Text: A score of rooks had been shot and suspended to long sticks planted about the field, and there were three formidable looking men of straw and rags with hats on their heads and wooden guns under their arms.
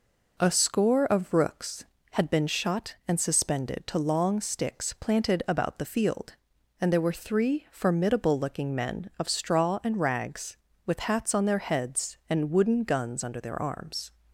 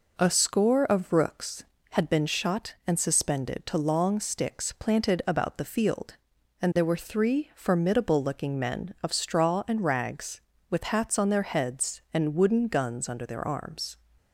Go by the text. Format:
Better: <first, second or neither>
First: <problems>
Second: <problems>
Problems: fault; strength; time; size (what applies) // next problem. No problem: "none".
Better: neither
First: none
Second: none